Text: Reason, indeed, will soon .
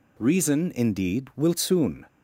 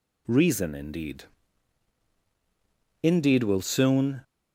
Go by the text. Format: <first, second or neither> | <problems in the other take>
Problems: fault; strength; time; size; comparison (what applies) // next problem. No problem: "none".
first | says "indeed" twice; at 3.0 s